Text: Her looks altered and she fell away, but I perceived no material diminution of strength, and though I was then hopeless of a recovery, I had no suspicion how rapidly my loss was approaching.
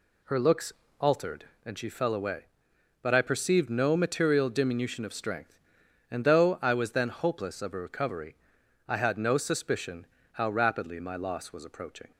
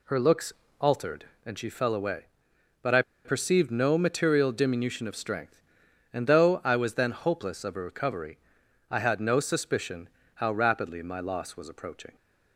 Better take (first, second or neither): first